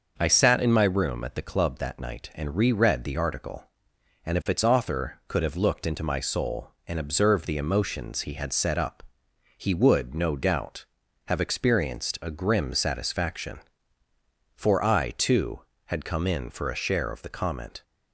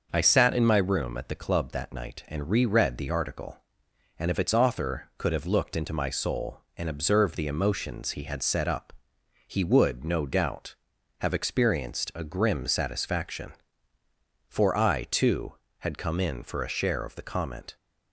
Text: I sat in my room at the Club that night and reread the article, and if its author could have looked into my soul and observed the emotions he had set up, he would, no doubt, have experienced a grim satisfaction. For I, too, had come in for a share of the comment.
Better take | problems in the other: neither | starts louder than the rest; noticeable; the same in both

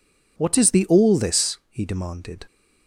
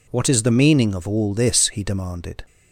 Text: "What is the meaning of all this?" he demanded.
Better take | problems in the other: second | skips "meaning of"; at 0.8 s

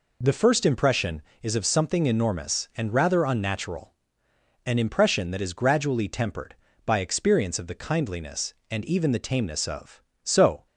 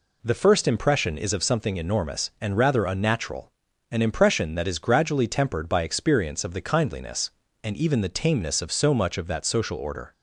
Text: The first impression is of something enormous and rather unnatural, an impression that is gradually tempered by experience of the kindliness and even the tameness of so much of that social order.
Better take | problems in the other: second | stops before "much of that social order"; at 10.6 s

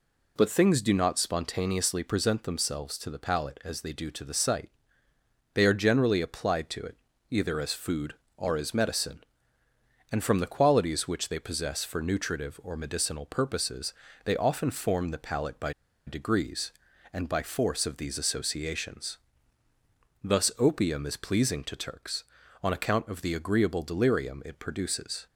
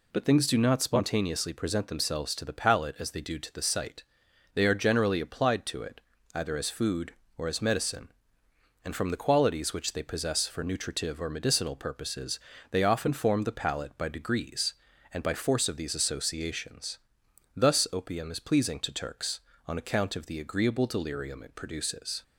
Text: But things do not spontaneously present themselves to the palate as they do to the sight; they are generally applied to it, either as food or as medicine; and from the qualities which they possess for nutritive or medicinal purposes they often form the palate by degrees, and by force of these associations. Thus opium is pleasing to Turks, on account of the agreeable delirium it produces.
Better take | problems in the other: second | pauses between "purposes" and "they"; slight; at 13.9 s; 0.30 s long; slight in the second // pauses between "by" and "degrees"; slight; at 15.7 s; 0.34 s long

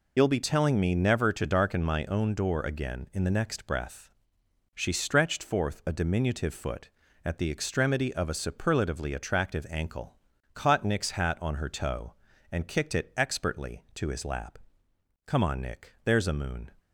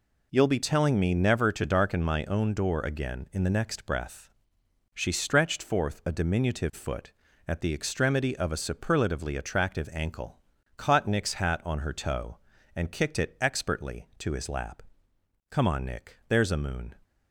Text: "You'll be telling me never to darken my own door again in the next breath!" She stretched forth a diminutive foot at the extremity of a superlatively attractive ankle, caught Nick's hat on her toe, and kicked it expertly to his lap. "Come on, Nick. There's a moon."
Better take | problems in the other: second | loses the start of "You'll"; at 0.1 s; 55 ms

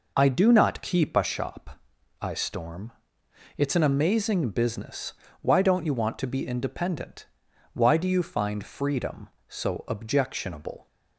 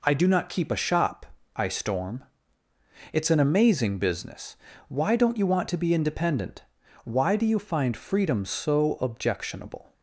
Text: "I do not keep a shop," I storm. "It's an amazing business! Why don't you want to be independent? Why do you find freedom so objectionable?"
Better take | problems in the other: neither | none

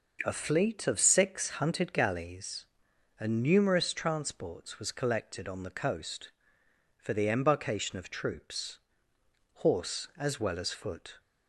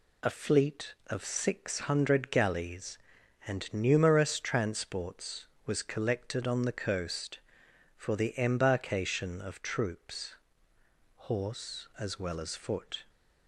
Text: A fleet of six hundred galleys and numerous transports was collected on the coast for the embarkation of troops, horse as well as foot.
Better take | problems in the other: second | says "hunted" for "hundred"; at 1.4 s

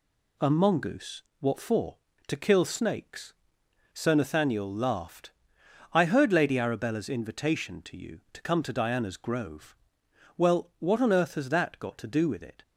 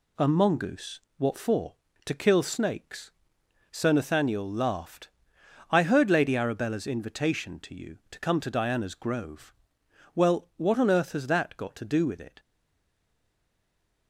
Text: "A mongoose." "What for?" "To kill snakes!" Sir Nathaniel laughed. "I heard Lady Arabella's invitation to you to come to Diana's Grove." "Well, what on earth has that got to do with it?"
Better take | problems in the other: first | stays silent after the last word; noticeable; from 12.3 s on; 1.7 s long

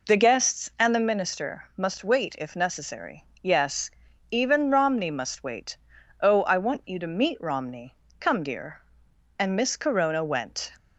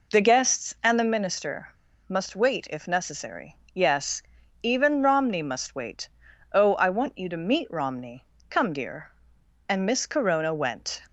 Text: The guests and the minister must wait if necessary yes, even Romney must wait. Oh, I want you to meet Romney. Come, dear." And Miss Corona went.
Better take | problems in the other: first | pauses between "minister" and "must"; at 1.6 s; 0.41 s long // pauses between "necessary" and "yes"; slight; at 3.5 s; 0.18 s long; slight in the first

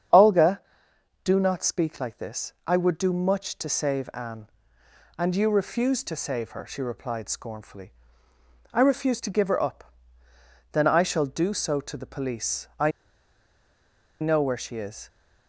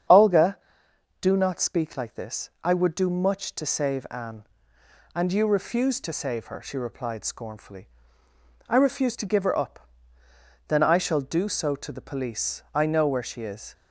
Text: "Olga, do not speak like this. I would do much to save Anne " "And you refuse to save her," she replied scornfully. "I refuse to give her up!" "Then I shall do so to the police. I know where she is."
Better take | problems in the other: second | starts louder than the rest; strong; until 1.7 s; 9 dB; strong in the second // pauses between "I" and "know"; strong; at 12.9 s; 1.3 s long

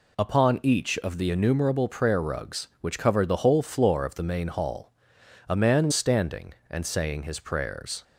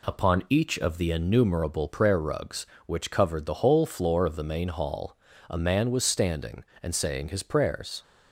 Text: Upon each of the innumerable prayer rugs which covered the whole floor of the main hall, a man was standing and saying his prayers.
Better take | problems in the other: second | skips "was"; at 5.9 s

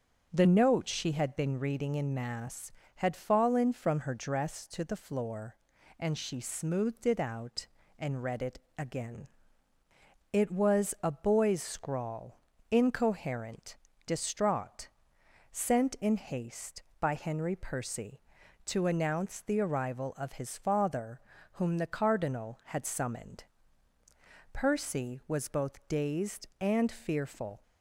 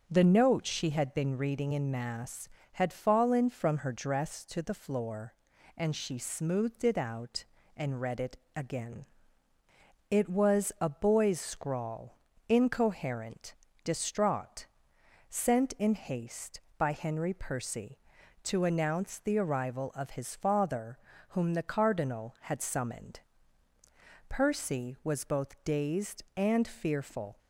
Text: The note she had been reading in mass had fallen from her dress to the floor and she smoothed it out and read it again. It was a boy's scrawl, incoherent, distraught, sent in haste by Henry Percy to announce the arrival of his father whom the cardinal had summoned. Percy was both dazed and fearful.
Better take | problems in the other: neither | starts louder than the rest; the same in both // pauses between "it" and "again"; slight; the same in both // pauses between "father" and "whom"; slight; the same in both

